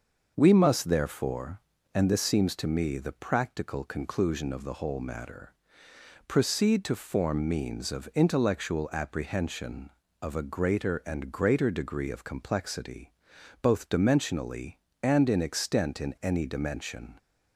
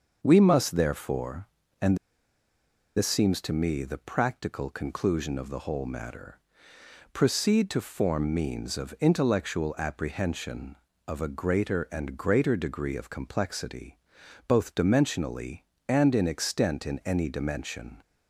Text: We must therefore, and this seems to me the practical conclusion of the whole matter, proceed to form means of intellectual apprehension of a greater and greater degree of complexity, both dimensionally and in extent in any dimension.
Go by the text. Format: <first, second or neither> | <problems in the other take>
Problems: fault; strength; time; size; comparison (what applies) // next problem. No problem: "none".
first | starts louder than the rest; until 1.2 s; 6.5 dB; also in the first // pauses between "and" and "this"; at 1.9 s; 0.98 s long